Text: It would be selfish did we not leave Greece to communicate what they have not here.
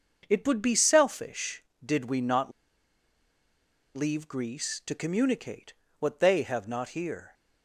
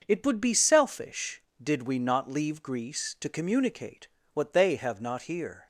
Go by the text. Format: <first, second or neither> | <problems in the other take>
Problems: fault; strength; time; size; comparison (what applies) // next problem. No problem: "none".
second | starts louder than the rest; noticeable; until 1.3 s; 6 dB; noticeable in the second // pauses between "not" and "leave"; strong; at 2.5 s; 1.4 s long // pauses between "communicate" and "what"; slight; at 5.7 s; 0.26 s long; slight in the second